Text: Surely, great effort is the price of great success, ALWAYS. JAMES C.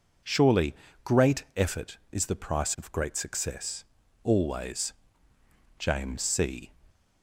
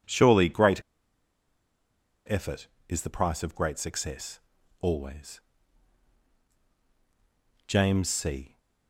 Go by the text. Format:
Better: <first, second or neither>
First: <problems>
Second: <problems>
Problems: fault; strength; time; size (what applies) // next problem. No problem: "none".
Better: first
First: none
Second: pauses between "great" and "effort"; strong; at 0.8 s; 1.4 s long